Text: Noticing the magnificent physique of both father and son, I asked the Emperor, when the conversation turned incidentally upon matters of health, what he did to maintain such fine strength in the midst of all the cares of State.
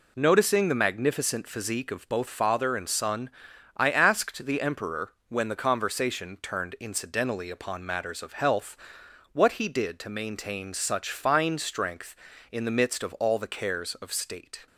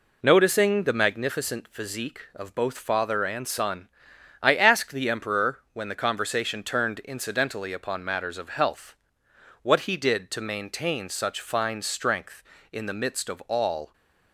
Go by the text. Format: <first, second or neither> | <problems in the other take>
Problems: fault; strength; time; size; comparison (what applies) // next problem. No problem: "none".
first | stops before "the cares of State"; at 13.9 s